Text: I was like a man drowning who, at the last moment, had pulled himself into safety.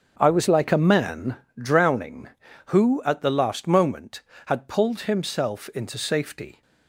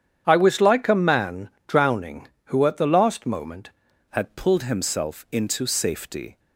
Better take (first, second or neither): first